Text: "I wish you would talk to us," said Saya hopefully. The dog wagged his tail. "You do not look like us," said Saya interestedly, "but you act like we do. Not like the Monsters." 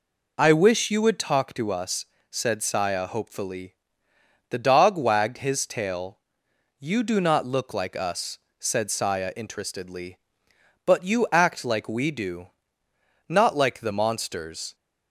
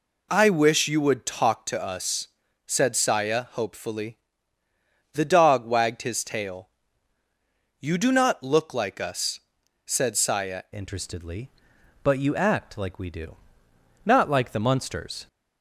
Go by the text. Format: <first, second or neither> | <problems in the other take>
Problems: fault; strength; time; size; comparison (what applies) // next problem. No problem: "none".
first | changes voice at "interestedly"; from 10.7 s on; 4.5 s long